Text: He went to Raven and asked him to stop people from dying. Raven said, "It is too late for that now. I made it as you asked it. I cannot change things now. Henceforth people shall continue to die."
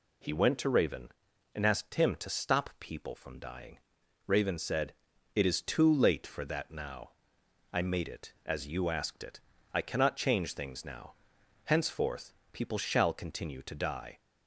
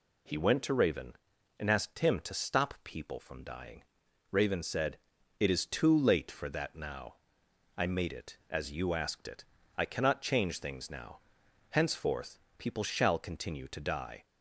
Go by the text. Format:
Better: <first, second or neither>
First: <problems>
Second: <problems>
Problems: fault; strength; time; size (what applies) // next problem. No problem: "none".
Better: neither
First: pauses between "Henceforth" and "people"; slight; at 12.3 s; 0.18 s long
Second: pauses between "Henceforth" and "people"; slight; at 12.3 s; 0.18 s long